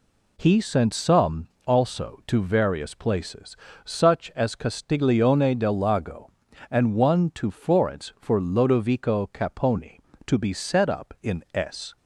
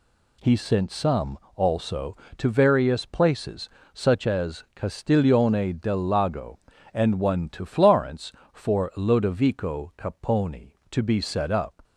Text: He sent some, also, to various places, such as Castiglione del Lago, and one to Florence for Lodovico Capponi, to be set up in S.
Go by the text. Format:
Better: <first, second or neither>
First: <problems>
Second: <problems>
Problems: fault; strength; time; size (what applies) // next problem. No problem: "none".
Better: first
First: none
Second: stops before "in S"; at 11.8 s